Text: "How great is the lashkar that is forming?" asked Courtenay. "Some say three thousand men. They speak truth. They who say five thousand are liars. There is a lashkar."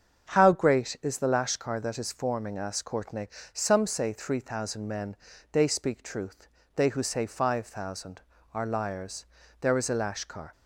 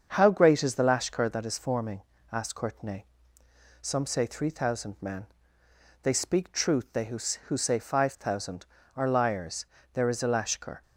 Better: first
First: starts louder than the rest; strong; until 1.3 s; 7.5 dB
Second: starts louder than the rest; until 1.1 s; 7 dB // says "who" twice; at 7.4 s

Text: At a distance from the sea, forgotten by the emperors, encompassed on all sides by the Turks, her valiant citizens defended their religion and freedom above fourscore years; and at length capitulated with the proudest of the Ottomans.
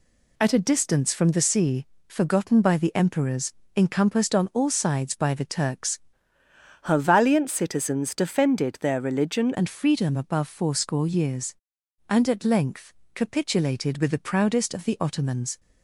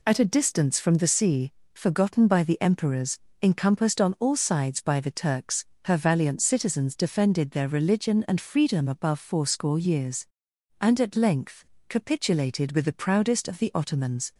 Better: second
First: changes voice from "her" to "religion"; from 6.8 to 9.5 s; 2.7 s long // pauses between "length" and "capitulated"; slight; at 12.9 s; 0.22 s long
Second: pauses between "length" and "capitulated"; slight; at 11.6 s; 0.24 s long

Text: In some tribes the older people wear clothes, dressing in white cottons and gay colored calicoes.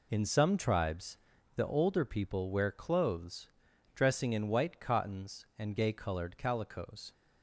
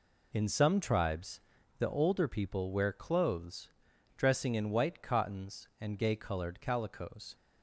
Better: neither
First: pauses between "tribes" and "the"; at 1.1 s; 0.38 s long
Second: pauses between "tribes" and "the"; at 1.3 s; 0.38 s long

